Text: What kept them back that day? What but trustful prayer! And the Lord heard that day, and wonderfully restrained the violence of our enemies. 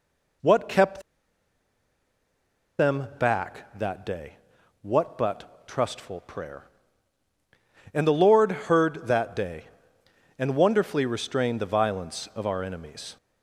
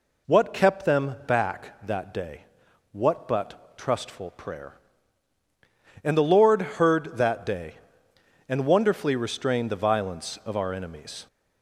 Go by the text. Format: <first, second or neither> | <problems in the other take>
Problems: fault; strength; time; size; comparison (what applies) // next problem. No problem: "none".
second | pauses between "kept" and "them"; strong; at 1.0 s; 1.7 s long